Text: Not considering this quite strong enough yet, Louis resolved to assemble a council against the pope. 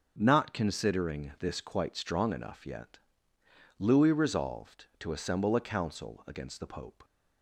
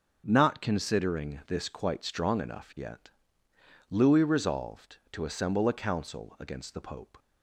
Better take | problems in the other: neither | starts louder than the rest; the same in both

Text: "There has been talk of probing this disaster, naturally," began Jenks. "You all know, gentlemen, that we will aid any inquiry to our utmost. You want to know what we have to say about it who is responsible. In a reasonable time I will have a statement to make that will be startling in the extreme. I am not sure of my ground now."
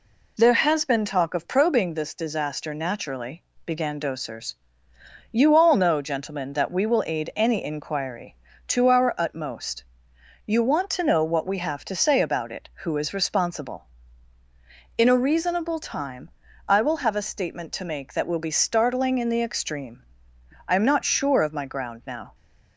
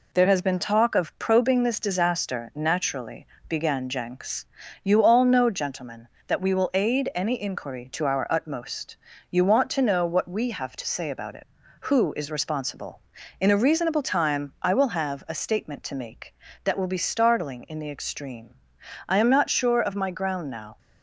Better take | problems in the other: second | says "Dosers" for "Jenks"; at 3.9 s // pauses between "time" and "I"; at 16.3 s; 0.38 s long

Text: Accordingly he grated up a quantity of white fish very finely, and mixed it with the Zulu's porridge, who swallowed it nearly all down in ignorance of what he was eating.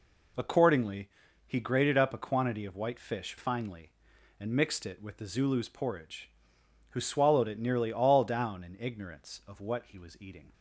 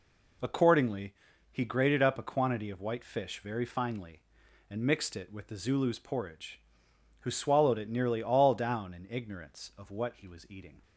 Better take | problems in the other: second | pauses between "Accordingly" and "he"; at 1.0 s; 0.38 s long; also in the second // skips "very"; at 3.3 s

